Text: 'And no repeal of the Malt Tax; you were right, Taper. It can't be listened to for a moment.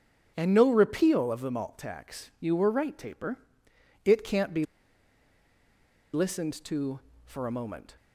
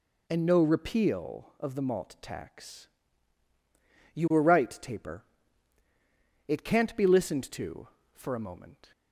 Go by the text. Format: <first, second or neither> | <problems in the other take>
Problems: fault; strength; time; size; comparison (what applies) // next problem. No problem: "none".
second | starts louder than the rest; strong; until 1.3 s; 8 dB // pauses between "be" and "listened"; strong; at 4.6 s; 1.4 s long